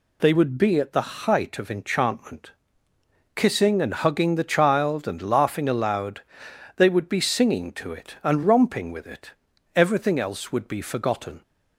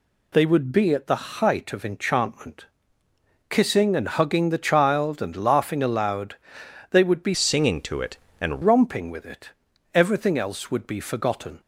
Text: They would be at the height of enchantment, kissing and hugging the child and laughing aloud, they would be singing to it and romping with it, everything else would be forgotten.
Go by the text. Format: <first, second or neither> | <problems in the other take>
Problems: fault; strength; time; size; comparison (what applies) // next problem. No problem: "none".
first | changes voice from "singing" to "and"; from 7.3 to 8.6 s; 1.3 s long